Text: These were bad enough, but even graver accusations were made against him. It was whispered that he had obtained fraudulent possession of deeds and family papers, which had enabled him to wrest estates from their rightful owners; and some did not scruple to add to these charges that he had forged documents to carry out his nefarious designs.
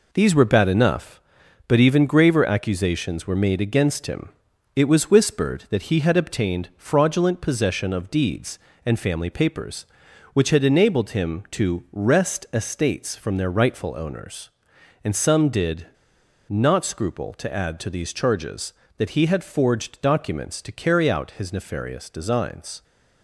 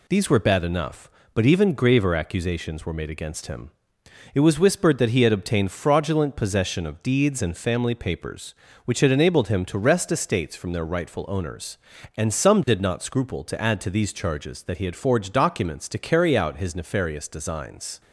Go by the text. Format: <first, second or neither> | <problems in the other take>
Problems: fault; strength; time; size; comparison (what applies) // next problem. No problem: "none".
second | pauses between "did" and "not"; noticeable; at 15.8 s; 0.60 s long